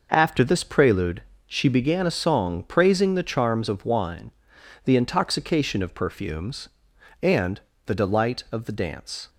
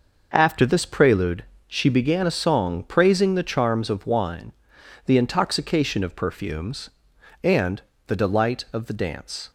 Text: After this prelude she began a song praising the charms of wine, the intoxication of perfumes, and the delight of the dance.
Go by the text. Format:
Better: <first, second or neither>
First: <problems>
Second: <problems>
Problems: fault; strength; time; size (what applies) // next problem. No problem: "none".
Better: neither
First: pauses between "prelude" and "she"; slight; at 1.2 s; 0.24 s long // pauses between "and" and "the"; slight; at 7.5 s; 0.26 s long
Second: pauses between "prelude" and "she"; slight; at 1.4 s; 0.22 s long // pauses between "and" and "the"; slight; at 7.8 s; 0.26 s long